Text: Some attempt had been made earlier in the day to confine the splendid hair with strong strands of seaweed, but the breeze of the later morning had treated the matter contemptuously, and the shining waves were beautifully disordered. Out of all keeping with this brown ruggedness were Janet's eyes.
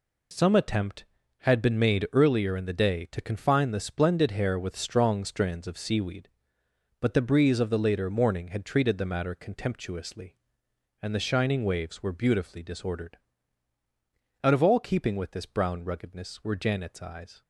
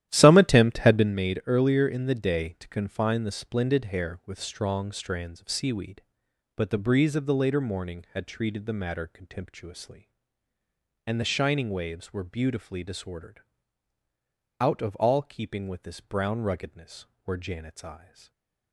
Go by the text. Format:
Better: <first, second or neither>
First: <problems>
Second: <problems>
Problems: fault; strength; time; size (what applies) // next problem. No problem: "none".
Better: first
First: none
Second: starts louder than the rest; strong; until 1.2 s; 12.5 dB // stays silent after the last word; slight; from 17.9 s on; 0.8 s long